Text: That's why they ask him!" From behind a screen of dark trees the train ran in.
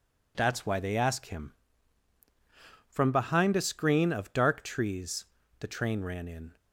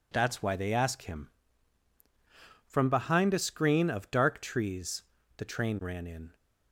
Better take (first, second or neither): neither